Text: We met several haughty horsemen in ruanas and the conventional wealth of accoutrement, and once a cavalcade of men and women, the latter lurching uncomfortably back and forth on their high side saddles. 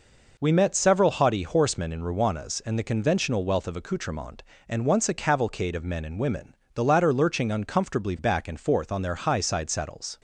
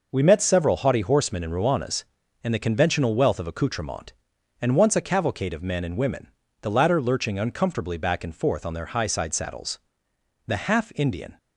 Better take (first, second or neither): first